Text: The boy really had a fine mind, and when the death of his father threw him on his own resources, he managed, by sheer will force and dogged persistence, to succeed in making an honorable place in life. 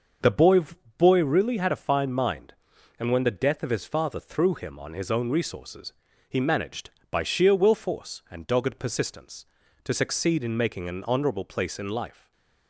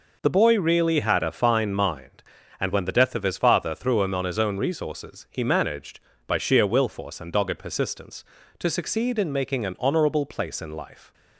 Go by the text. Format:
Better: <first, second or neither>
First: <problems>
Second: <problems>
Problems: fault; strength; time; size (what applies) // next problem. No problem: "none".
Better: second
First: starts louder than the rest; until 1.6 s; 6.5 dB // says "boy" twice; at 0.9 s // stays silent after the last word; slight; from 12.1 s on; 0.5 s long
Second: none